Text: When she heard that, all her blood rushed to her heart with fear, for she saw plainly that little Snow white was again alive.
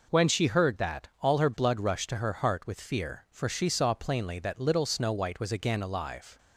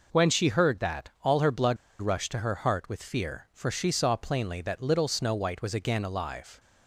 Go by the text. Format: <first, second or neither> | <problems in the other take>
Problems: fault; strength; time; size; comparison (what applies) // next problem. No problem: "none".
first | pauses between "blood" and "rushed"; slight; at 1.7 s; 0.25 s long